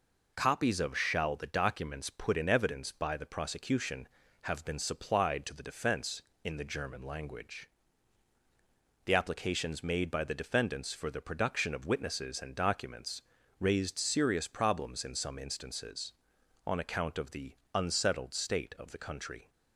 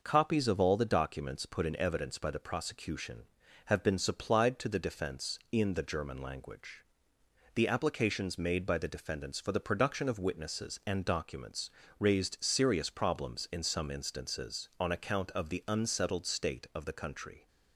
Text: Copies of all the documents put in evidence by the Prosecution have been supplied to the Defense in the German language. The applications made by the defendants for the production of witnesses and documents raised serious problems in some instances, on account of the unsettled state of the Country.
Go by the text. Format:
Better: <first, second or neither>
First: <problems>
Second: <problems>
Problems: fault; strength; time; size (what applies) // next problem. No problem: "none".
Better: second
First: says "shall" for "all"; at 0.9 s // pauses between "documents" and "raised"; at 13.2 s; 0.38 s long // pauses between "the" and "unsettled"; slight; at 17.5 s; 0.18 s long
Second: pauses between "documents" and "raised"; slight; at 11.6 s; 0.30 s long